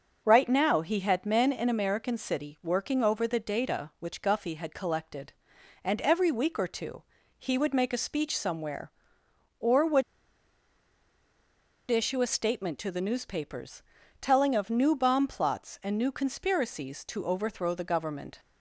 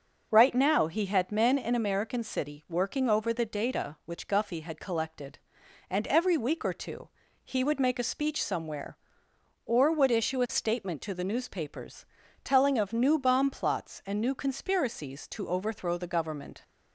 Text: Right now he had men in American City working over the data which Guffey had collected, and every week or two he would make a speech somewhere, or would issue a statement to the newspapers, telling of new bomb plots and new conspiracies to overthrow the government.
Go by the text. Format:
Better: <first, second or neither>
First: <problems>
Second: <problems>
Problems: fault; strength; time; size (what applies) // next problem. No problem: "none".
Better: second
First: starts louder than the rest; until 1.2 s; 6.5 dB // pauses between "two" and "he"; slight; at 7.0 s; 0.34 s long // pauses between "would" and "issue"; strong; at 10.0 s; 1.8 s long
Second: starts louder than the rest; until 1.3 s; 6.5 dB // pauses between "two" and "he"; slight; at 7.0 s; 0.34 s long